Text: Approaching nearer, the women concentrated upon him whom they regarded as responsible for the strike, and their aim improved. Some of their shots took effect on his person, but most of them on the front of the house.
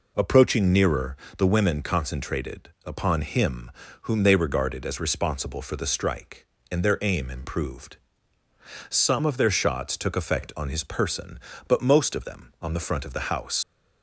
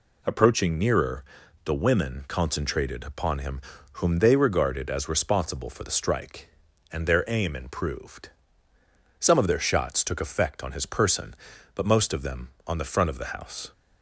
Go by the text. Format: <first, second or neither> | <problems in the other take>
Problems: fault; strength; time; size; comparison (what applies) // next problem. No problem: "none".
second | pauses between "concentrated" and "upon"; slight; at 2.6 s; 0.18 s long // pauses between "him" and "whom"; slight; at 3.7 s; 0.30 s long; slight in the second // leaves "house" unfinished; at 13.6 s; 90 ms